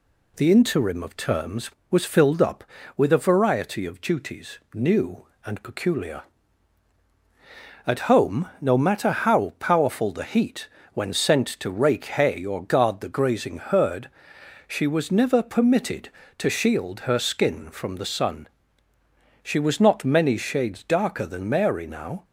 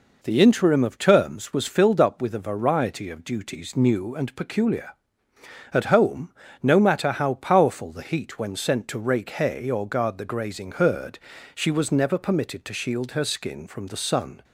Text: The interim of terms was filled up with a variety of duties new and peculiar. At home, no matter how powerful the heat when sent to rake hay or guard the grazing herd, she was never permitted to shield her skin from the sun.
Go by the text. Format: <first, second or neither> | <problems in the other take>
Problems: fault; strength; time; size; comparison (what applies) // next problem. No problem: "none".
second | pauses between "duties" and "new"; slight; at 4.5 s; 0.16 s long // pauses between "heat" and "when"; slight; at 10.6 s; 0.26 s long // goes on to say "She was not many shades darker than Mary now"; strong; from 19.4 s on; 2.8 s long